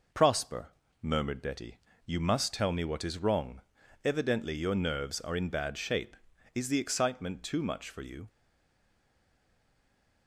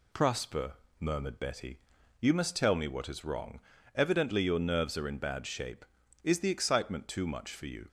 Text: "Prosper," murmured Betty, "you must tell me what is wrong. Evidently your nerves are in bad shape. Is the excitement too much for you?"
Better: second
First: stays silent after the last word; noticeable; from 8.2 s on; 2.0 s long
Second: none

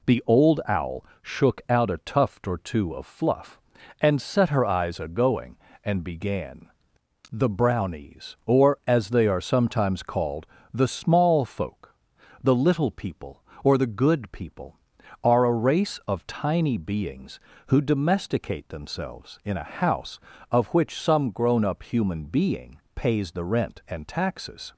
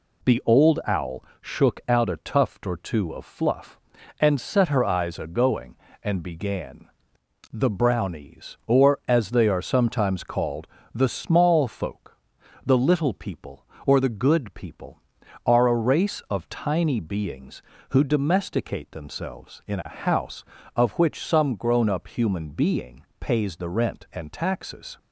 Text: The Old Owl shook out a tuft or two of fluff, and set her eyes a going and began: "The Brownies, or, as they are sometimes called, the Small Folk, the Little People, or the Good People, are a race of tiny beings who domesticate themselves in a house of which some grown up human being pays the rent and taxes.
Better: neither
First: pauses between "Owl" and "shook"; slight; at 1.0 s; 0.16 s long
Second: pauses between "Owl" and "shook"; slight; at 1.2 s; 0.16 s long

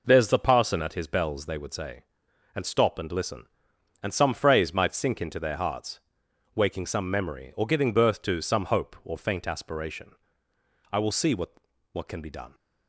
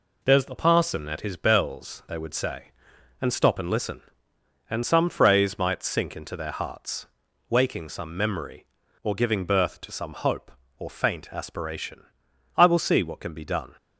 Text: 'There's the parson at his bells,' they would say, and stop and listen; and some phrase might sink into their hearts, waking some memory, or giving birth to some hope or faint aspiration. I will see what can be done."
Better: second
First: says "what" twice; at 11.9 s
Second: none

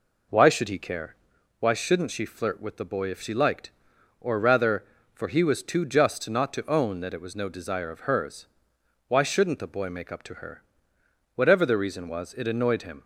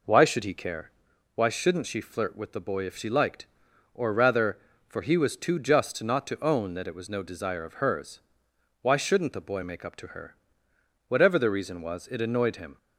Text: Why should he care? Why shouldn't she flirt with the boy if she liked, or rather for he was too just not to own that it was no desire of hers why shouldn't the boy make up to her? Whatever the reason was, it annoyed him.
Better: neither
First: pauses between "hers" and "why"; noticeable; at 8.4 s; 0.62 s long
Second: pauses between "hers" and "why"; noticeable; at 8.1 s; 0.62 s long

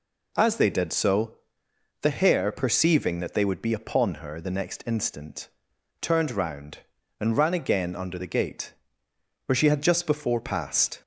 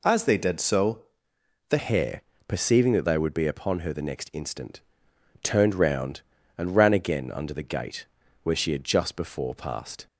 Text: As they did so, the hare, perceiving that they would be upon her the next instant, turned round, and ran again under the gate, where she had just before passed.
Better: first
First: none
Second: changes voice at "hare"; from 1.7 s on; 8.3 s long

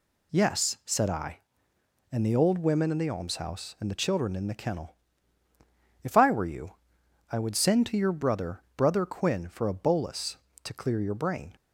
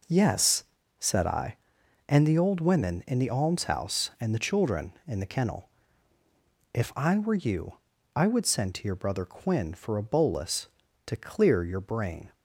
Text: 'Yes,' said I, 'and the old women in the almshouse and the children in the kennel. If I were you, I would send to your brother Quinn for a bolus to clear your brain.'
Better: second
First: says "brother" twice; at 8.7 s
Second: none

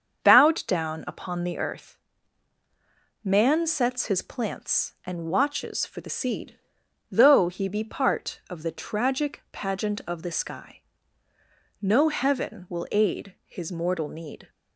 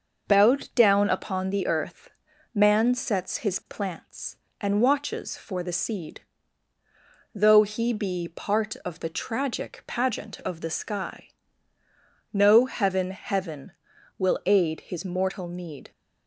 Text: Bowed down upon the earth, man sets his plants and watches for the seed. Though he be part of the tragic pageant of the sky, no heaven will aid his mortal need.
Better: first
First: starts louder than the rest; until 1.3 s; 7 dB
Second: starts louder than the rest; noticeable; until 1.3 s; 6 dB // says "heaven" twice; at 13.1 s

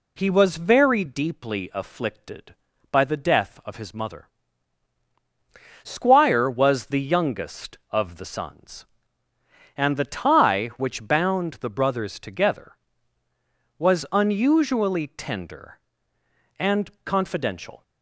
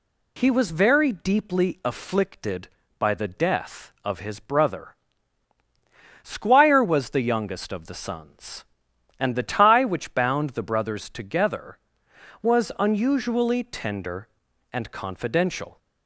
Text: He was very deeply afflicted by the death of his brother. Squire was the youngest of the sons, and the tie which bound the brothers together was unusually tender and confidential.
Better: second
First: says "mother" for "brother"; at 3.9 s // pauses between "and" and "confidential"; slight; at 16.8 s; 0.16 s long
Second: none

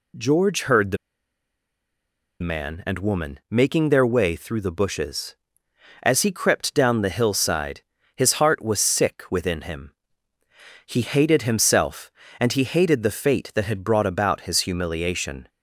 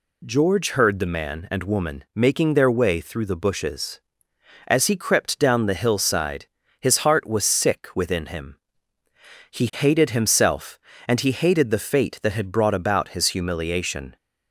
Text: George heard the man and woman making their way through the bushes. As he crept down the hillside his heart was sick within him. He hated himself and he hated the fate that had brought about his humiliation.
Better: second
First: pauses between "the" and "man"; strong; at 0.9 s; 1.4 s long // pauses between "hillside" and "his"; slight; at 7.8 s; 0.34 s long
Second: pauses between "hillside" and "his"; slight; at 6.4 s; 0.34 s long

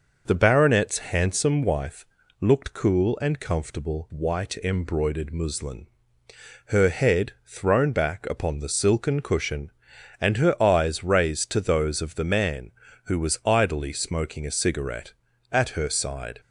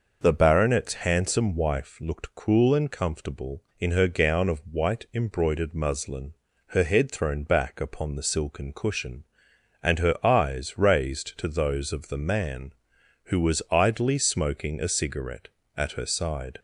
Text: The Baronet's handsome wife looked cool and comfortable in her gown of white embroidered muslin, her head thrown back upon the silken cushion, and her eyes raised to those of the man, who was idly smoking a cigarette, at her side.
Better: second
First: pauses between "Baronet's" and "handsome"; slight; at 0.9 s; 0.16 s long // pauses between "wife" and "looked"; slight; at 2.0 s; 0.36 s long // skips "in her gown of"; at 4.1 s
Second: none

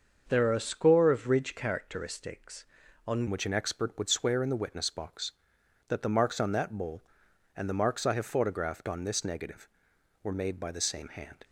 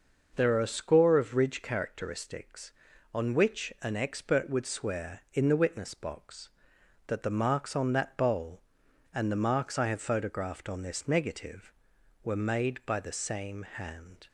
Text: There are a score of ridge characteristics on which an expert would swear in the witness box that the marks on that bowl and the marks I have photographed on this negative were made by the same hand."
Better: second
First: starts louder than the rest; until 1.2 s; 6 dB // changes voice at "which"; from 3.2 s on; 8.2 s long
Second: none

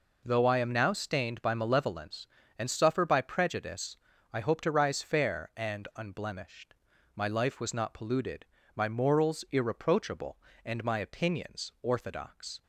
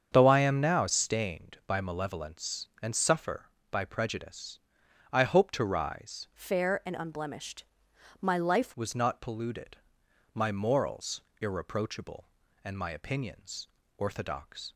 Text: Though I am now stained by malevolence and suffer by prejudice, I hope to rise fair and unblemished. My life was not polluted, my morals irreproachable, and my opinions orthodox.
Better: first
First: none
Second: starts louder than the rest; strong; until 1.1 s; 7 dB // changes voice from "fair" to "life"; from 6.3 to 8.7 s; 2.4 s long // pauses between "morals" and "irreproachable"; slight; at 11.2 s; 0.18 s long // pauses between "opinions" and "orthodox"; slight; at 13.6 s; 0.30 s long

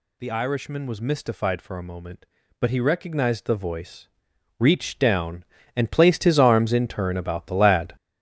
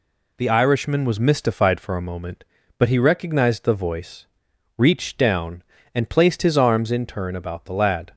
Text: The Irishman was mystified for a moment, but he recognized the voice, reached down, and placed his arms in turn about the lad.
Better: second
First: gets louder; strong; throughout; 7.5 dB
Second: none

